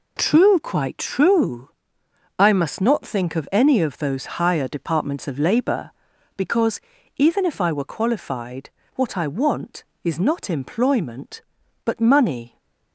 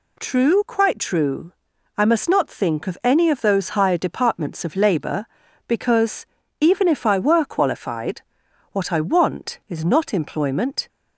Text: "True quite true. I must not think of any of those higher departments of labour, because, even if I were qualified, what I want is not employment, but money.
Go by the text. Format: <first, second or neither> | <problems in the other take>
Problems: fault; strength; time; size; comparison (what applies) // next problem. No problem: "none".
first | stops before "but money"; at 10.8 s